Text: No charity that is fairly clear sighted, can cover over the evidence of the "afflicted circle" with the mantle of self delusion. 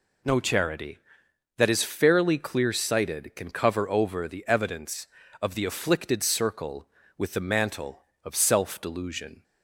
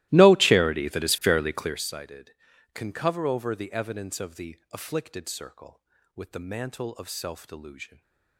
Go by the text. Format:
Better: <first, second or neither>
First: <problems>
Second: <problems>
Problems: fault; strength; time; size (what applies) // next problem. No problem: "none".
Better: first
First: none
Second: starts louder than the rest; strong; until 1.9 s; 17 dB // stays silent after the last word; slight; from 7.8 s on; 0.5 s long